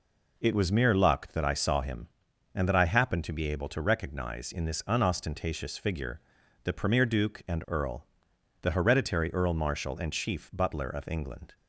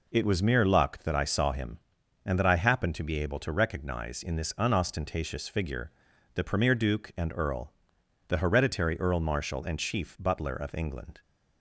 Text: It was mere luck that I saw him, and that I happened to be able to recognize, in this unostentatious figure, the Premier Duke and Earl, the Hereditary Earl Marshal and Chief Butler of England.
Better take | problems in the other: neither | none

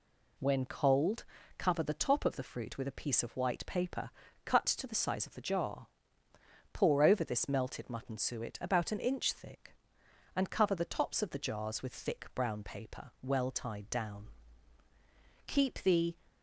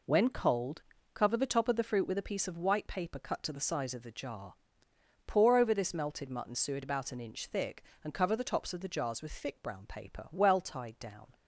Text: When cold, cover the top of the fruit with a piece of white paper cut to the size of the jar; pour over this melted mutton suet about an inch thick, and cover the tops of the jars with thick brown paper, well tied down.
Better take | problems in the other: second | pauses between "paper" and "cut"; slight; at 4.1 s; 0.34 s long // goes on to say "Keep the"; noticeable; from 15.4 s on; 0.68 s long

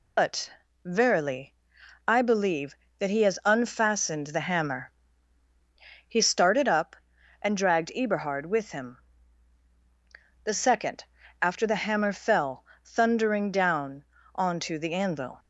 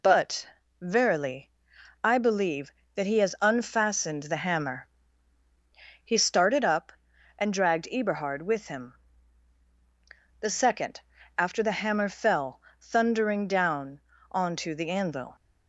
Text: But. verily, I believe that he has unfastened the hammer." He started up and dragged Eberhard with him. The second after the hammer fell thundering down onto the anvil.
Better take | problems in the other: second | loses the start of "But"; at 0.1 s; 105 ms // pauses between "second" and "after"; slight; at 11.0 s; 0.36 s long; slight in the second // pauses between "fell" and "thundering"; slight; at 12.6 s; 0.18 s long; slight in the second // pauses between "down" and "onto"; slight; at 14.0 s; 0.30 s long; slight in the second

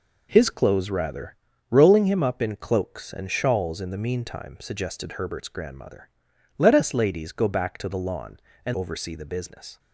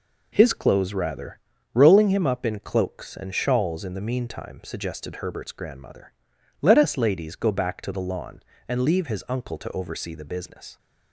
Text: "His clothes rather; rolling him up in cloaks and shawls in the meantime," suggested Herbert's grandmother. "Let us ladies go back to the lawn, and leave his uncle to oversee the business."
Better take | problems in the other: second | skips "leave his uncle to"; at 8.7 s

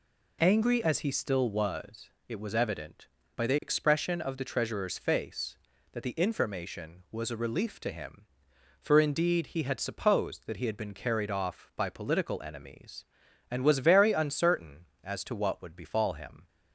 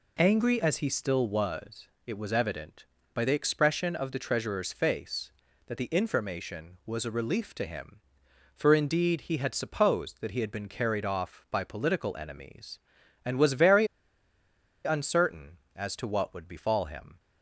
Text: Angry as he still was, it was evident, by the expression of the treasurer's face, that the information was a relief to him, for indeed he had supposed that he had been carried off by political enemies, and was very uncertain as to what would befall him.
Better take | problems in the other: first | pauses between "very" and "uncertain"; at 13.8 s; 0.99 s long

